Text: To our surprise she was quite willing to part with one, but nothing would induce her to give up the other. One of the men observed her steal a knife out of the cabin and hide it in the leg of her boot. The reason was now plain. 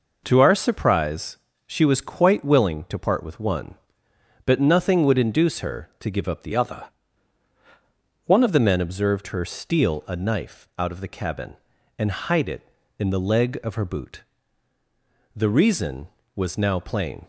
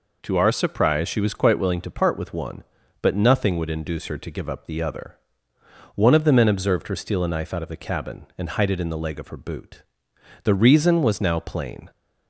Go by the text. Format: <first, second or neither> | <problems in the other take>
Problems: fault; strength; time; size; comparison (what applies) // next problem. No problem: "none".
second | pauses between "surprise" and "she"; slight; at 1.3 s; 0.28 s long // changes voice from "other" to "One"; from 6.5 to 8.4 s; 1.9 s long